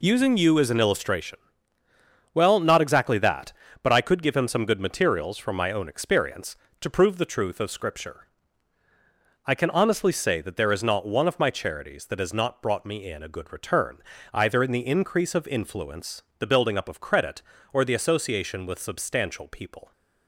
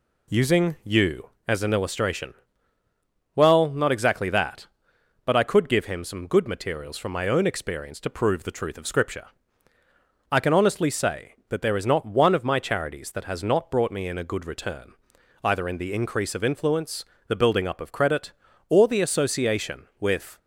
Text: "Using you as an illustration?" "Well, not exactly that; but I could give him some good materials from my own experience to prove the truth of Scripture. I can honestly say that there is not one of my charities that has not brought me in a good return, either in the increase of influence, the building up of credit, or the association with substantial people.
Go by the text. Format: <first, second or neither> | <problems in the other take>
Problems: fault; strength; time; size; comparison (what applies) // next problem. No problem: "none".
first | stops before "substantial people"; at 20.3 s